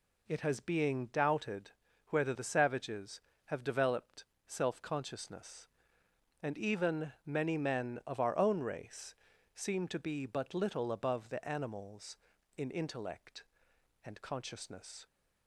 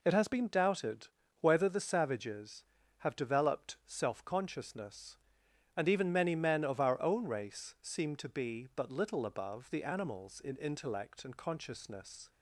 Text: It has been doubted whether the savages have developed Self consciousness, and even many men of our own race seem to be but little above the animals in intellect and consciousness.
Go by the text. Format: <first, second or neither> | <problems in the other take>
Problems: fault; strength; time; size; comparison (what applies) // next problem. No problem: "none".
second | says "being" for "been"; at 0.5 s // pauses between "doubted" and "whether"; at 1.6 s; 0.38 s long; slight in the second // pauses between "developed" and "Self"; slight; at 4.2 s; 0.22 s long // pauses between "race" and "seem"; at 9.1 s; 0.41 s long